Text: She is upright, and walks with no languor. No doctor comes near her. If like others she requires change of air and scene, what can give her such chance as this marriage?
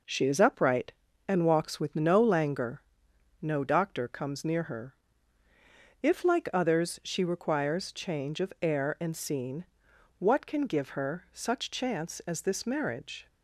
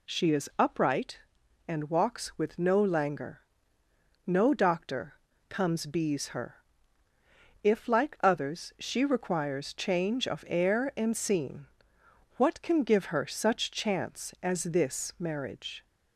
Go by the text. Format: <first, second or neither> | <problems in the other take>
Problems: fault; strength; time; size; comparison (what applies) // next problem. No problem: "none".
first | pauses between "doctor" and "comes"; slight; at 5.1 s; 0.34 s long // says "bees" for "near"; at 5.8 s